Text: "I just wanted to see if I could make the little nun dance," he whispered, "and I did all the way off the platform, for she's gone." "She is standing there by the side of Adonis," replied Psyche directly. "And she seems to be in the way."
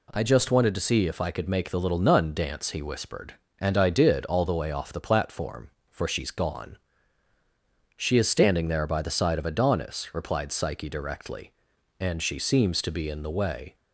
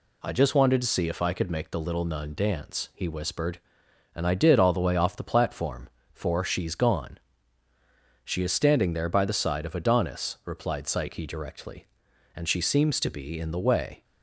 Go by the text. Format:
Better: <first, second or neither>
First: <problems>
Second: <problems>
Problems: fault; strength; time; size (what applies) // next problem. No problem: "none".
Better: neither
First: none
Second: none